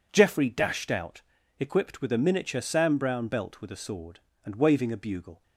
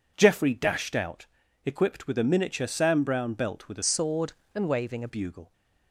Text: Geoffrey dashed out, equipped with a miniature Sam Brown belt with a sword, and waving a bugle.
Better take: first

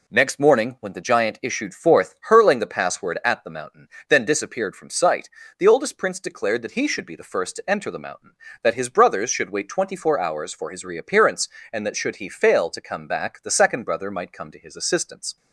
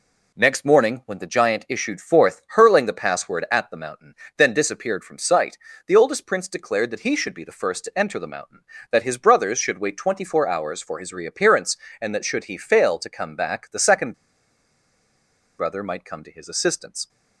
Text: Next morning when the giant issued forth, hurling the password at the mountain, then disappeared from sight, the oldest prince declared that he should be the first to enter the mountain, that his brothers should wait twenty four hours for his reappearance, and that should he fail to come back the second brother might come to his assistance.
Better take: first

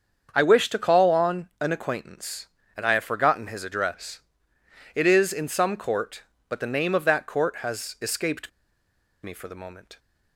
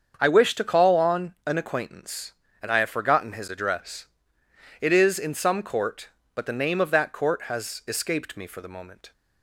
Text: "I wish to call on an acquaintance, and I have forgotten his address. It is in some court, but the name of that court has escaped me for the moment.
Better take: second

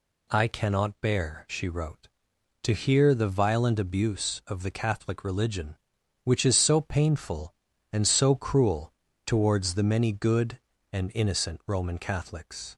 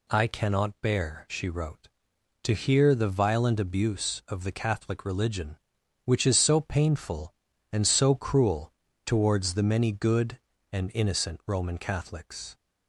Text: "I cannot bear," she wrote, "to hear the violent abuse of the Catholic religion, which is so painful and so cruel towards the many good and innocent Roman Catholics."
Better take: neither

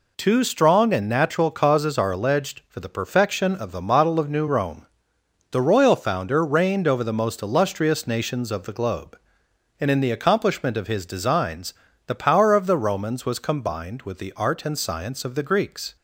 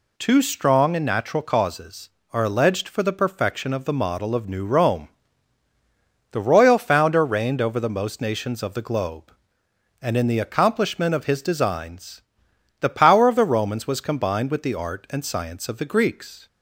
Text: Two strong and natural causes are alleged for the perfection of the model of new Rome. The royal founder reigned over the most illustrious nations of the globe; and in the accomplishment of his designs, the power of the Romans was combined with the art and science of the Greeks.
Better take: first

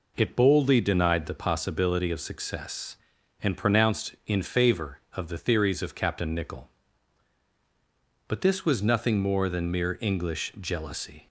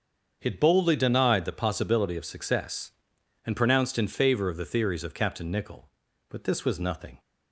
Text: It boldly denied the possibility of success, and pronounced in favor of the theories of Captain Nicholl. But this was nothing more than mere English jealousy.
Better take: first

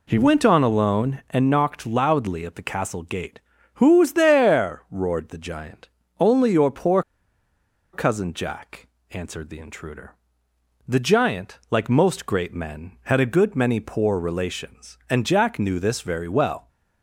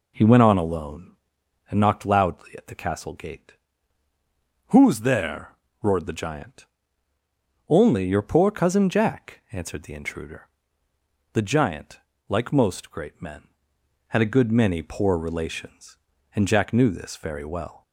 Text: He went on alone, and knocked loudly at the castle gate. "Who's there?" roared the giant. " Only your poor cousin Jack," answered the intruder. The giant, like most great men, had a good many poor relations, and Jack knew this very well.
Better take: second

